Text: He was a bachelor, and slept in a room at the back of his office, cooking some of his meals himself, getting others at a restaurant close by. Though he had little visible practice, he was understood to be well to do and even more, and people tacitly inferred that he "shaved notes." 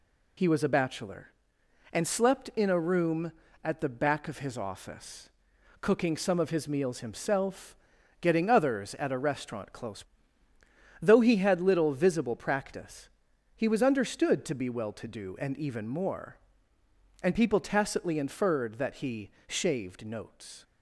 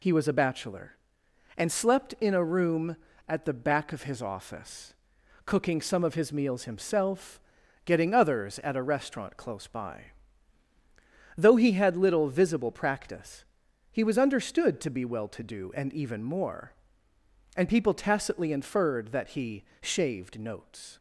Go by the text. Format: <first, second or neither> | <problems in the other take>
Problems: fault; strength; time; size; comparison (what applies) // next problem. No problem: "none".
second | skips "by"; at 10.5 s // pauses between "he" and "shaved"; slight; at 19.3 s; 0.18 s long; slight in the second